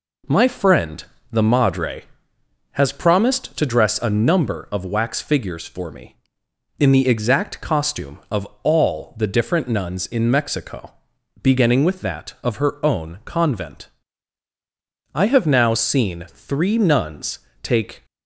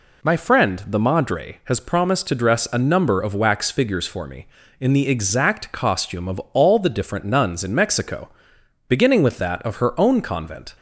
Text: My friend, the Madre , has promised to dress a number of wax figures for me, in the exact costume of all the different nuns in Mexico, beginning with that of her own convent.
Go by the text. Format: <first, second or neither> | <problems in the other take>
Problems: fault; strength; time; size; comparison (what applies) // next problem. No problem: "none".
second | pauses between "of" and "all"; slight; at 8.4 s; 0.16 s long; slight in the second // goes on to say "I have now seen three nuns take"; strong; from 15.1 s on; 2.9 s long